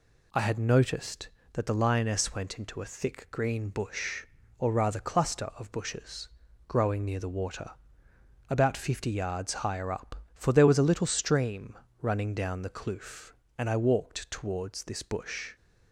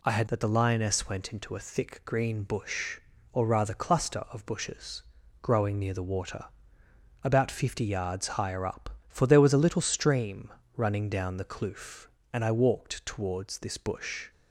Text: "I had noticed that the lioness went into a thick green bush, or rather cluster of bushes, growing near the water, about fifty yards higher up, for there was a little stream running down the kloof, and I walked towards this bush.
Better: first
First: pauses between "stream" and "running"; slight; at 11.7 s; 0.24 s long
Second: skips "noticed"; at 0.2 s // pauses between "stream" and "running"; slight; at 10.5 s; 0.24 s long

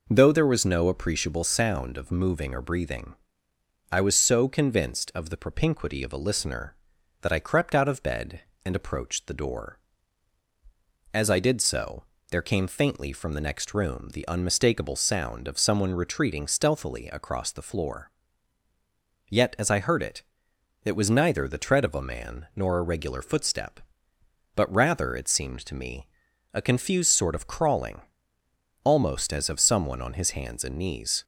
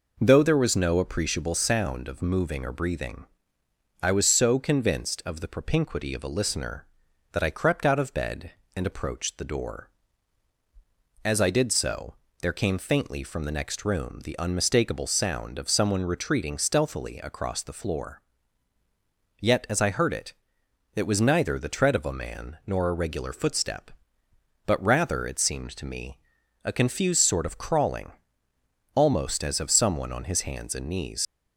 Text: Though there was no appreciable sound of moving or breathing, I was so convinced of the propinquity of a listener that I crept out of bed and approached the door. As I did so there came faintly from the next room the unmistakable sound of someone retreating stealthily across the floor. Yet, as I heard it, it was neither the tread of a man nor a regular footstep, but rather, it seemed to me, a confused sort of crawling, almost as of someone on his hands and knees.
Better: first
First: pauses between "so" and "there"; slight; at 12.0 s; 0.26 s long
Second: pauses between "so" and "there"; slight; at 12.1 s; 0.26 s long // leaves "knees" unfinished; at 31.2 s; 90 ms

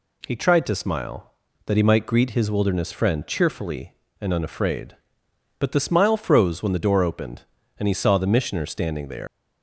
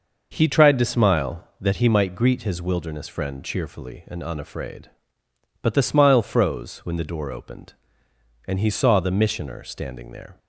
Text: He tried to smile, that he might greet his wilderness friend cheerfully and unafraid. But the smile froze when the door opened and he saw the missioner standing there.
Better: second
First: leaves "there" unfinished; at 9.2 s; 135 ms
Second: none

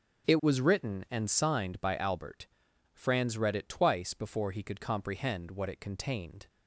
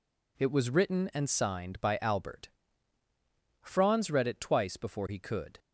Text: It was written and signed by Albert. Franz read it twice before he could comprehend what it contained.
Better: first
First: none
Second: stops before "comprehend what it contained"; at 5.5 s

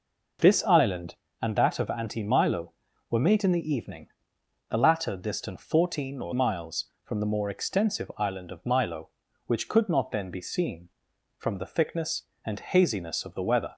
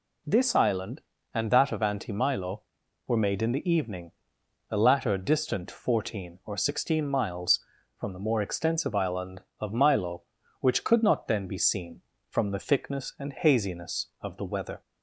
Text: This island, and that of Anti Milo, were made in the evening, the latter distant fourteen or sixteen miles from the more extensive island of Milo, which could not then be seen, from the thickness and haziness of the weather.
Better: second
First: skips "sixteen"; at 6.3 s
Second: none

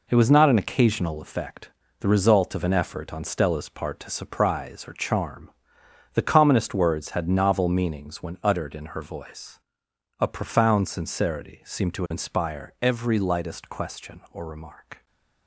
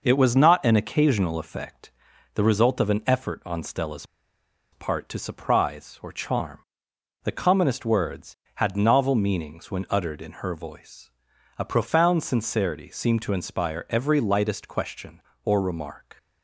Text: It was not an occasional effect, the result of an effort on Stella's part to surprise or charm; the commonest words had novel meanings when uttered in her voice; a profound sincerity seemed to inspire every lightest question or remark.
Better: first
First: none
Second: pauses between "Stella's" and "part"; noticeable; at 4.0 s; 0.66 s long

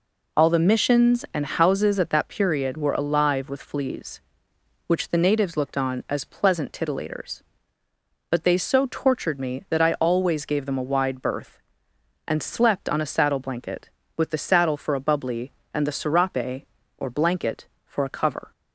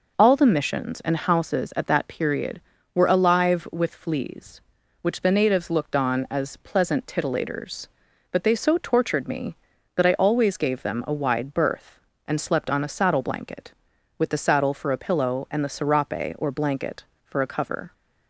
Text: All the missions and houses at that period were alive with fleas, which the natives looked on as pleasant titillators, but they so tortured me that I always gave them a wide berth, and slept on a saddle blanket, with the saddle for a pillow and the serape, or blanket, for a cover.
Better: second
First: says "bubbly" for "pillow"; at 14.9 s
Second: none

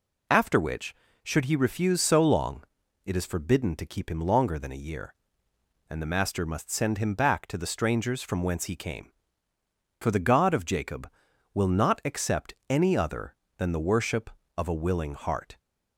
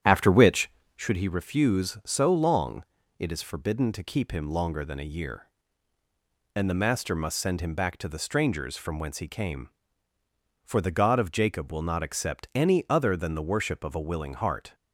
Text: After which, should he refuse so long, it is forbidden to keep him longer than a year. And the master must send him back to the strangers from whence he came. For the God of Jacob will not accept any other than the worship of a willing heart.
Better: first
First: none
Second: starts louder than the rest; strong; until 1.2 s; 9.5 dB

